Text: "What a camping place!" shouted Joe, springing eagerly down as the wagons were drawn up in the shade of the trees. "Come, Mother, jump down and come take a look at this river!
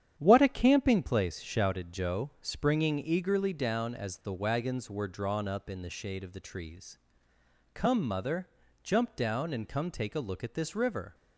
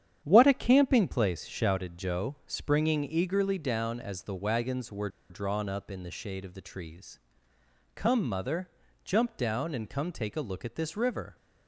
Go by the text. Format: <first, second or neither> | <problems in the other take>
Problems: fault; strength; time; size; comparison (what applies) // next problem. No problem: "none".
first | starts louder than the rest; strong; until 1.2 s; 9 dB; strong in the first // pauses between "were" and "drawn"; slight; at 5.0 s; 0.21 s long